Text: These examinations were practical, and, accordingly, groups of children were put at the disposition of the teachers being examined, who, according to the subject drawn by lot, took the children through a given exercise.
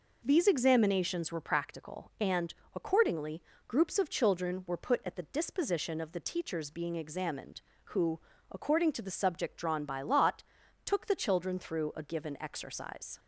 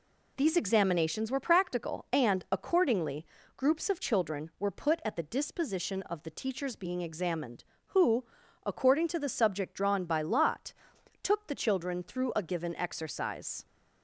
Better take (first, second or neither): neither